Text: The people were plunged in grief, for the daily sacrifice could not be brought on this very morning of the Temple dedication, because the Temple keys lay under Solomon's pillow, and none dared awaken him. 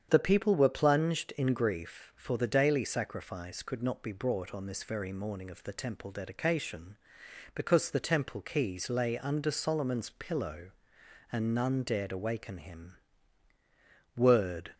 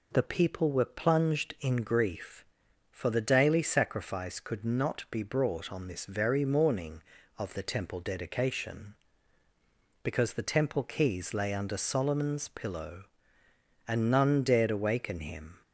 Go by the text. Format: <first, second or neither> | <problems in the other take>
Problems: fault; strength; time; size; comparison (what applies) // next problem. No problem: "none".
second | starts louder than the rest; strong; until 1.1 s; 8.5 dB // goes on to say "Word"; from 14.1 s on; 0.58 s long